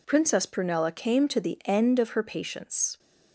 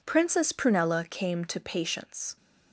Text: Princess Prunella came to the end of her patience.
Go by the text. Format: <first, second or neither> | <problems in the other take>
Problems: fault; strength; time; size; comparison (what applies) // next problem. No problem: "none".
first | skips "the end of her"; at 1.5 s